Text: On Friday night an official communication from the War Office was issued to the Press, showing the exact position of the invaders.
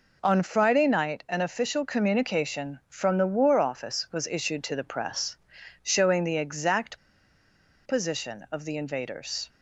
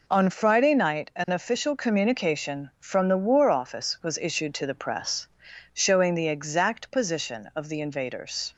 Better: second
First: pauses between "exact" and "position"; noticeable; at 6.9 s; 0.87 s long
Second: none

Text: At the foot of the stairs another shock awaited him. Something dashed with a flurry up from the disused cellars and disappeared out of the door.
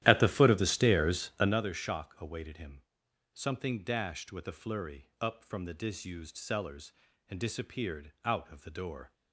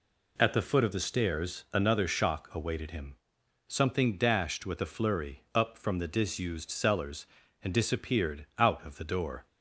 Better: second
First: starts louder than the rest; strong; until 1.7 s; 13 dB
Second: none

